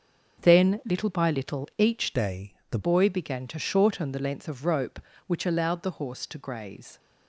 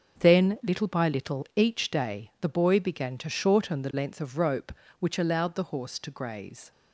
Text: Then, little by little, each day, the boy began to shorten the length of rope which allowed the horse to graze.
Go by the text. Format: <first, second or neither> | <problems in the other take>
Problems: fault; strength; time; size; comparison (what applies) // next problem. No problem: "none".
second | starts louder than the rest; until 1.5 s; 6.5 dB; also in the second // changes voice from "day" to "the"; from 2.1 to 2.7 s; 0.6 s long